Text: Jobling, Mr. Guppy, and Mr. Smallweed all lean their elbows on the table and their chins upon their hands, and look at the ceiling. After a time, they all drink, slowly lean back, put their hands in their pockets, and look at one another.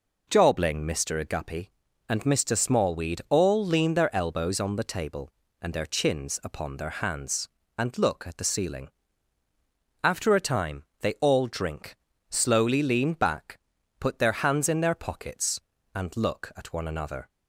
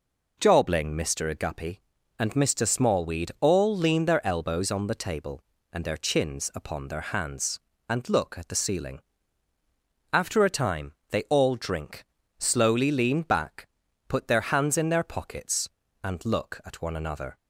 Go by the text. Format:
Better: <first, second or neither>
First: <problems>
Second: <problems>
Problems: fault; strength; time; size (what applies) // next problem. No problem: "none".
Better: neither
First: none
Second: none